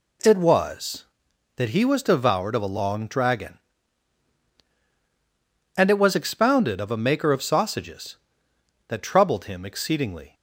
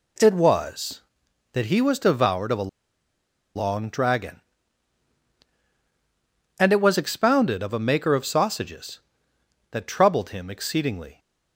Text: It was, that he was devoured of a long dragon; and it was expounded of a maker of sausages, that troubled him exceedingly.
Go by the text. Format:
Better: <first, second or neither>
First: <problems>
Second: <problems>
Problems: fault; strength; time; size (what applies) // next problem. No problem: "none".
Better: first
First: none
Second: pauses between "a" and "long"; noticeable; at 2.6 s; 0.87 s long